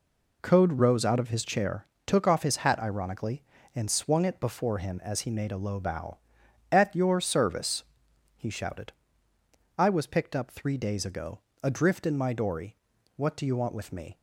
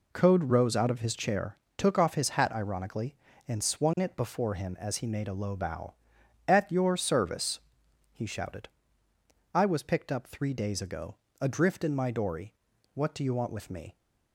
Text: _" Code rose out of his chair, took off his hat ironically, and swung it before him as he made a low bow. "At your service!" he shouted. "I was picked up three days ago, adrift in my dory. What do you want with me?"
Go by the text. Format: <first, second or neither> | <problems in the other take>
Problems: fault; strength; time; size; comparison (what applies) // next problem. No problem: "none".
neither | none